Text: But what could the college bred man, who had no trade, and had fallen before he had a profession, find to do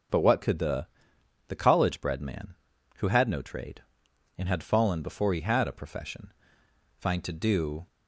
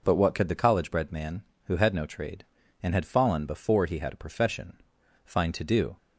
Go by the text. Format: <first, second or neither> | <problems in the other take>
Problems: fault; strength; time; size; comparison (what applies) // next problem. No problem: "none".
second | says "the" twice; at 1.4 s